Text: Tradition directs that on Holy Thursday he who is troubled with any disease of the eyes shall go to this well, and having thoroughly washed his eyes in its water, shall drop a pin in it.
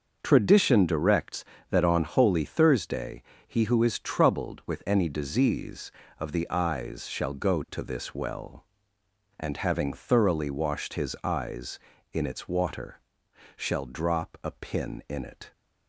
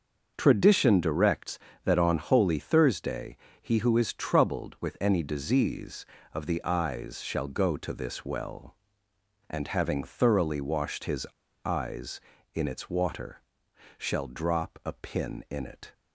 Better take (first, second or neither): first